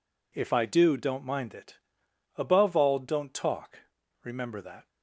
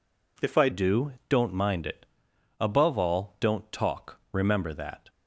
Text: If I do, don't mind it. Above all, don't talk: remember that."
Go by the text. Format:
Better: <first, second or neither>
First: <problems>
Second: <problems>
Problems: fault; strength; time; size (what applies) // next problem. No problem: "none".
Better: first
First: none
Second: changes voice at "do"; from 0.7 s on; 4.3 s long